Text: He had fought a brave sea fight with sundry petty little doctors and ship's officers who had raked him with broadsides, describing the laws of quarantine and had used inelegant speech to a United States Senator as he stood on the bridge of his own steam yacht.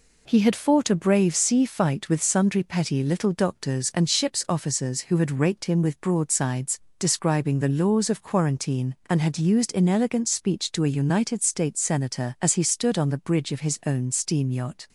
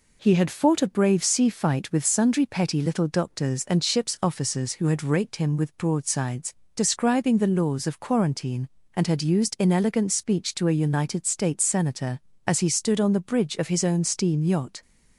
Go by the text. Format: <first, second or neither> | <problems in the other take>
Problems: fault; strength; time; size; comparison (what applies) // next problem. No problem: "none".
neither | none